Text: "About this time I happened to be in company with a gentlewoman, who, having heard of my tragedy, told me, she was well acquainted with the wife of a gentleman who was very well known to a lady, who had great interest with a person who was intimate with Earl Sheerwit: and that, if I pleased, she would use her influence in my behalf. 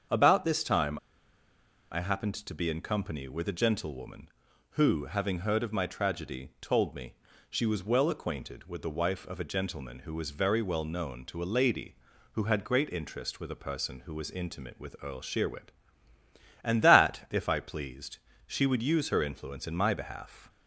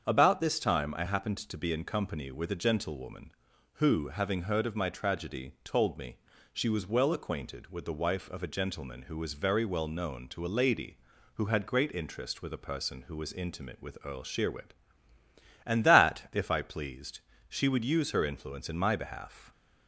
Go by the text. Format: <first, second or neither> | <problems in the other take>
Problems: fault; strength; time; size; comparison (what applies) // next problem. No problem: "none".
second | starts louder than the rest; strong; until 2.0 s; 7 dB; strong in the second // pauses between "time" and "I"; noticeable; at 0.9 s; 0.93 s long